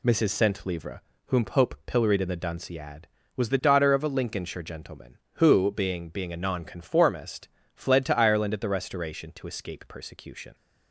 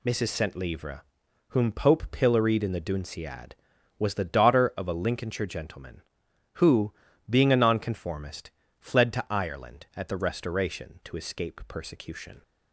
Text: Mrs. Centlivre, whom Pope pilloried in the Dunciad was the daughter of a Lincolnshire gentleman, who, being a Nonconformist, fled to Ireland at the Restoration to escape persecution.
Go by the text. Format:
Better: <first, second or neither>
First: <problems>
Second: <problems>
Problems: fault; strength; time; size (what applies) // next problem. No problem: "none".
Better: second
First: says "being" twice; at 6.0 s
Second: none